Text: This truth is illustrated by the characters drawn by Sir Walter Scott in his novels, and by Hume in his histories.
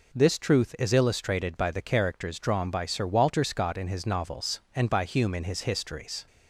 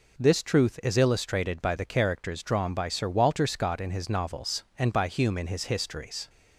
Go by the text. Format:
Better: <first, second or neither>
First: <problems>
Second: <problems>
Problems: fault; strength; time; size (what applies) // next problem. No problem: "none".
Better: neither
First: none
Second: none